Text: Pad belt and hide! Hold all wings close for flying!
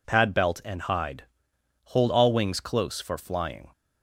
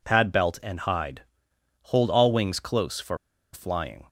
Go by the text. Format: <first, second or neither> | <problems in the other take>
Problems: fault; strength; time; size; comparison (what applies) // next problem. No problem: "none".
first | pauses between "for" and "flying"; at 3.1 s; 0.36 s long